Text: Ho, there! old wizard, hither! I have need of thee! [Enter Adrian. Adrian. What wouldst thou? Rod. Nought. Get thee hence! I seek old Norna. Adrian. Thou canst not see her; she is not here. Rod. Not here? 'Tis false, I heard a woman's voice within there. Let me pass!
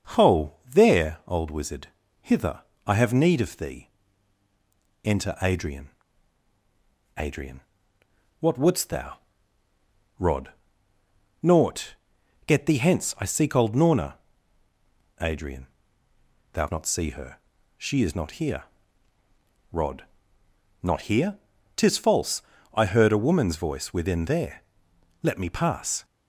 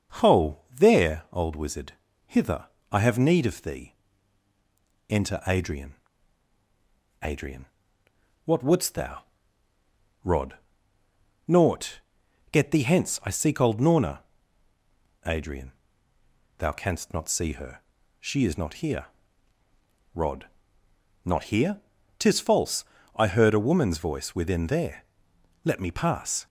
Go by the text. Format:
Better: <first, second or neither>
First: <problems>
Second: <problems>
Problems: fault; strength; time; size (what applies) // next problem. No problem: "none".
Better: second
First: starts louder than the rest; noticeable; until 1.3 s; 6 dB // skips "canst"; at 16.6 s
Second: starts louder than the rest; noticeable; until 1.4 s; 6 dB